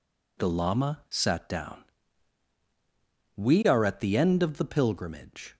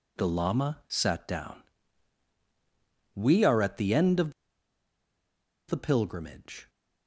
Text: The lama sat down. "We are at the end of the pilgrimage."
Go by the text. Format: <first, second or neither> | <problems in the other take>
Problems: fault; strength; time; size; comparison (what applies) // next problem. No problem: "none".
first | pauses between "of" and "the"; strong; at 4.3 s; 1.3 s long